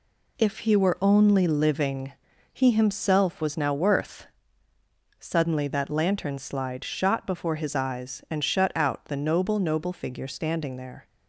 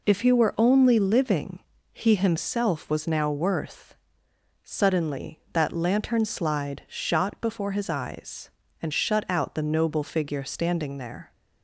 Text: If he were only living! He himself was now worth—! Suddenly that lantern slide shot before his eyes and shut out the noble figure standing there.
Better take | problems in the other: second | says "noble" twice; at 9.5 s

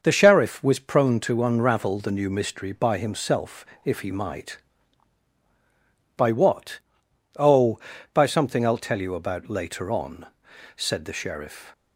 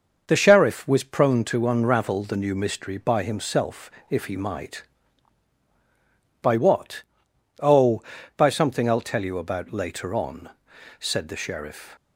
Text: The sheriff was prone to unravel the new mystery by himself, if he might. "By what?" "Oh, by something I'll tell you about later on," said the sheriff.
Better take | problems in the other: neither | starts louder than the rest; noticeable; the same in both

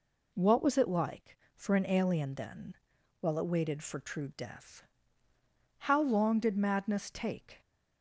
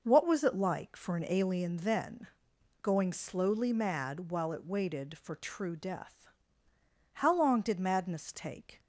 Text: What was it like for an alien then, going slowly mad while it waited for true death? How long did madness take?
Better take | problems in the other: second | skips "going slowly mad"; at 2.9 s

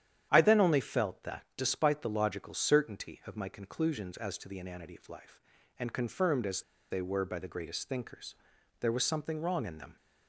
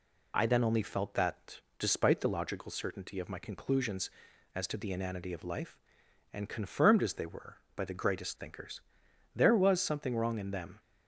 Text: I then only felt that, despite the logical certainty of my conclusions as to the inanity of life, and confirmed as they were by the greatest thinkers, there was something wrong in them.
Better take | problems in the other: second | starts louder than the rest; strong; until 1.3 s; 10 dB // pauses between "as" and "they"; slight; at 6.6 s; 0.27 s long

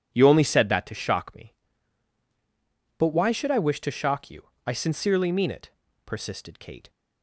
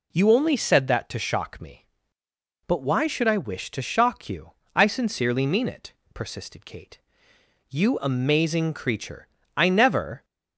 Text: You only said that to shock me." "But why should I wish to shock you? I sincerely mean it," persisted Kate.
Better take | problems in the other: first | goes on to say "You amazing creature I never"; strong; from 7.6 s on; 2.5 s long

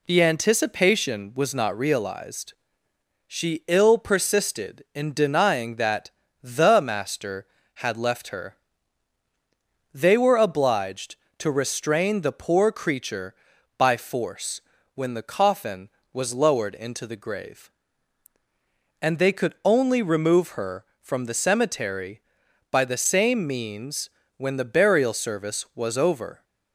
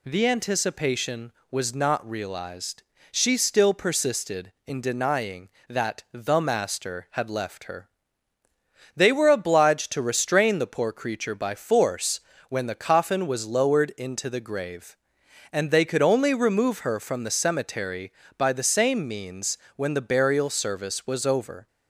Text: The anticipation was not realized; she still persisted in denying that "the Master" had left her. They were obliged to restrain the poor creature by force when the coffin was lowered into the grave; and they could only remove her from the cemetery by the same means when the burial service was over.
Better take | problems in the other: second | says "ill" for "still"; at 3.6 s // pauses between "that" and "the"; slight; at 6.0 s; 0.32 s long // pauses between "force" and "when"; slight; at 14.5 s; 0.34 s long; slight in the second // pauses between "means" and "when"; slight; at 24.0 s; 0.26 s long; slight in the second

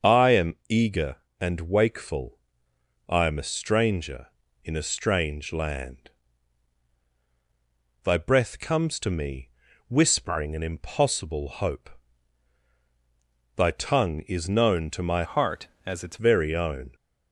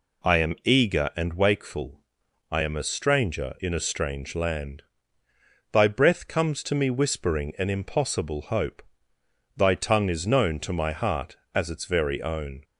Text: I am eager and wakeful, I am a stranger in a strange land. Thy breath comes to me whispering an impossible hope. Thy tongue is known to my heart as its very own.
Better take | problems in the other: second | starts louder than the rest; until 1.4 s; 6.5 dB // pauses between "am" and "eager"; slight; at 0.5 s; 0.16 s long // pauses between "me" and "whispering"; at 9.4 s; 0.38 s long // changes voice from "heart" to "its"; from 15.2 to 16.1 s; 0.9 s long

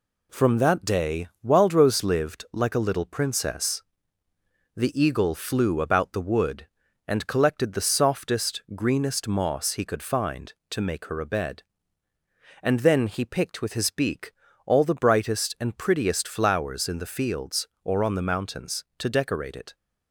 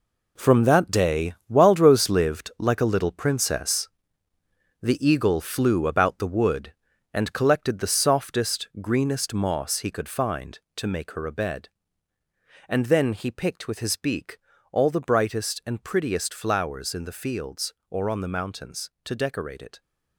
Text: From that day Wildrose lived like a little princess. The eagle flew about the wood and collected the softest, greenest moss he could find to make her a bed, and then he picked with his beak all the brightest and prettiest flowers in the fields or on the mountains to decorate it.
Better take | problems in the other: first | gets quieter; strong; throughout; 10.5 dB // pauses between "day" and "Wildrose"; slight; at 1.3 s; 0.16 s long; slight in the first // pauses between "beak" and "all"; slight; at 14.3 s; 0.34 s long; slight in the first

